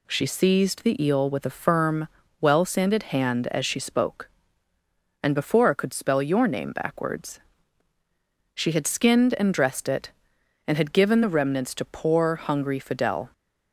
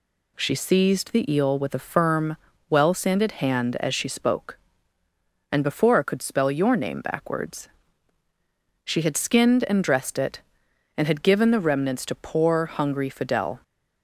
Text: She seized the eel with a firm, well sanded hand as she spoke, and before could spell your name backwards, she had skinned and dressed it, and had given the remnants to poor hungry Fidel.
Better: neither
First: none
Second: none

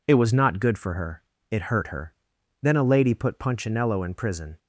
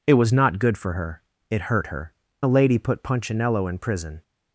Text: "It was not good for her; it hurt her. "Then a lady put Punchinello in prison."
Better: first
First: none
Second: skips "Then"; at 2.2 s

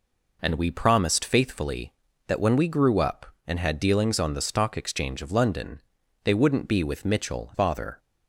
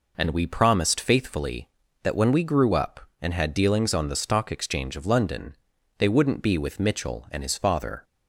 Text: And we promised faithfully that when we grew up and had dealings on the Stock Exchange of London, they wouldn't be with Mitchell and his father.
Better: second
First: skips "and his"; at 7.5 s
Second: none

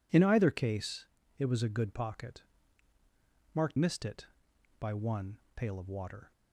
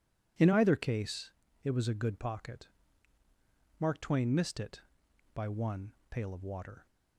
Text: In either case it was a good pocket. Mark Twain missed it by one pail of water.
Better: second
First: pauses between "case" and "it"; slight; at 1.0 s; 0.34 s long // skips "Twain"; at 3.7 s // pauses between "one" and "pail"; slight; at 5.3 s; 0.18 s long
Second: pauses between "case" and "it"; slight; at 1.2 s; 0.34 s long // pauses between "one" and "pail"; slight; at 5.9 s; 0.18 s long

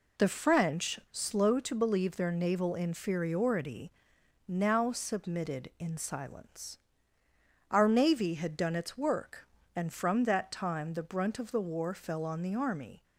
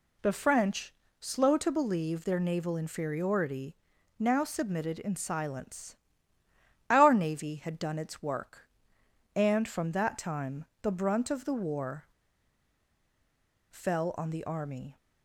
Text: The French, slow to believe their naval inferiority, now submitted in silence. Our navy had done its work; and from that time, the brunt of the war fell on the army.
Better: first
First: none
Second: pauses between "war" and "fell"; strong; at 12.0 s; 1.6 s long

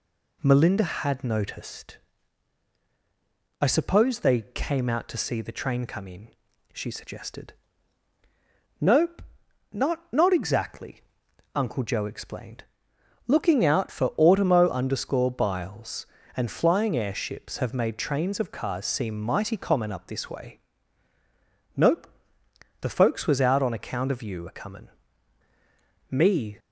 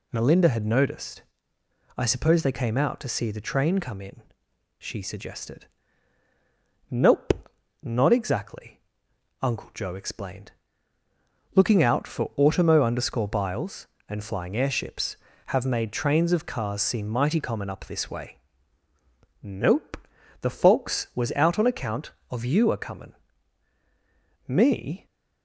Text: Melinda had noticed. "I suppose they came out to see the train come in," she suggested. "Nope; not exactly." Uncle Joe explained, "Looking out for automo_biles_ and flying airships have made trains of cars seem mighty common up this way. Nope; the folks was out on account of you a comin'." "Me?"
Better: second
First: says "not" twice; at 10.1 s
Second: none

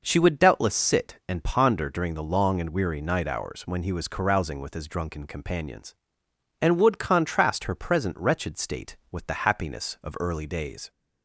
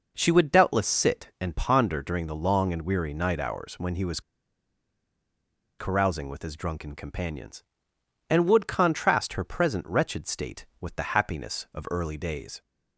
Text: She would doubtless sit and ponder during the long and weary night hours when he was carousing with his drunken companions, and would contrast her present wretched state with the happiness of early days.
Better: first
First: none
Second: pauses between "was" and "carousing"; strong; at 4.2 s; 1.5 s long

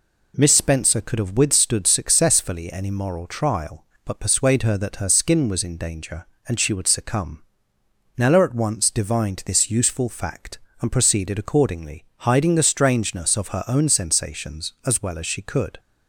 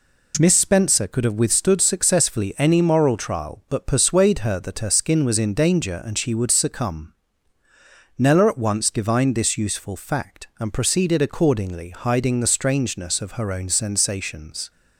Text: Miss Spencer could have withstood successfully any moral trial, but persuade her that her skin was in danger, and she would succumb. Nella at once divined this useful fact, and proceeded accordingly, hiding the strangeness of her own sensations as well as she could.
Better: first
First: none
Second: stops before "as well as she could"; at 14.6 s

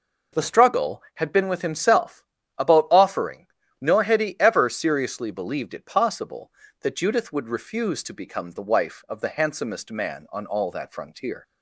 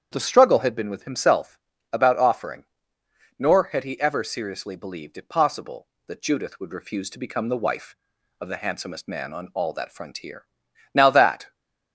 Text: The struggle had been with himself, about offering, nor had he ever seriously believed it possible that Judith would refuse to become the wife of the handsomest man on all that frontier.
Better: first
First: none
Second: starts louder than the rest; strong; until 1.1 s; 8.5 dB // goes on to say "Now that"; from 10.9 s on; 0.60 s long

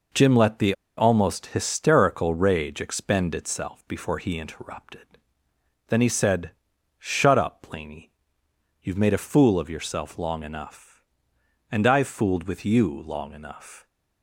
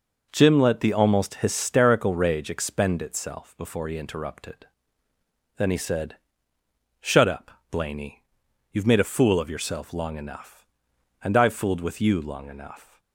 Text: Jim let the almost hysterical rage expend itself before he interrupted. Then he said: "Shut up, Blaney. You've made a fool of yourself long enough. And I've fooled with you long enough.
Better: second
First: pauses between "the" and "almost"; slight; at 0.7 s; 0.23 s long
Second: none

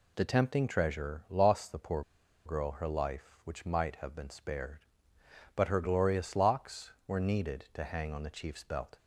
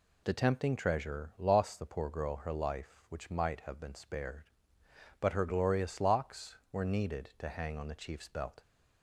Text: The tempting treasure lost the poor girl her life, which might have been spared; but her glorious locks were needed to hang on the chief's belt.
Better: second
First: pauses between "poor" and "girl"; at 2.0 s; 0.44 s long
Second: none

